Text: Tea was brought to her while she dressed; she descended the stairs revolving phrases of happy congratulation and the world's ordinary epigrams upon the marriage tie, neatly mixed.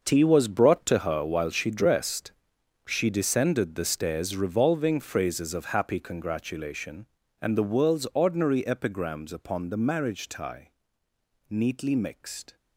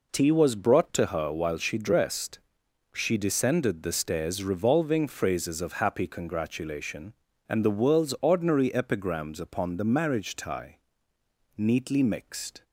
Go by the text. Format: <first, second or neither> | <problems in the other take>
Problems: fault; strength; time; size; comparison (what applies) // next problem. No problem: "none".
second | gets quieter; strong; throughout; 12.5 dB